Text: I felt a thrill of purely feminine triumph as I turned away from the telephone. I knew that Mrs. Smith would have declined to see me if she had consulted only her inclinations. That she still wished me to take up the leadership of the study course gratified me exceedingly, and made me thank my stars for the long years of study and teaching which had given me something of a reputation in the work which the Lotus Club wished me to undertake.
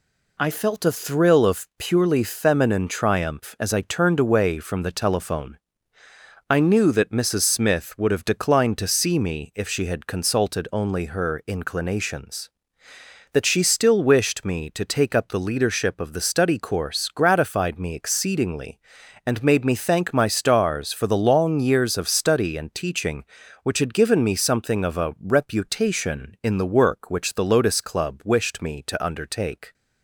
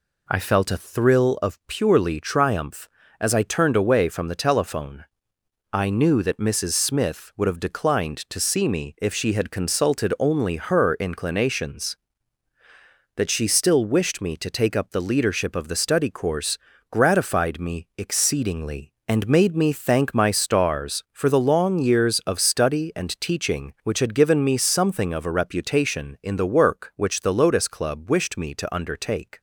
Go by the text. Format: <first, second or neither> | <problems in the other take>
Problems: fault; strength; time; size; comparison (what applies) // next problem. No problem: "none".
first | skips "feminine"; at 2.1 s // pauses between "course" and "gratified"; slight; at 16.5 s; 0.32 s long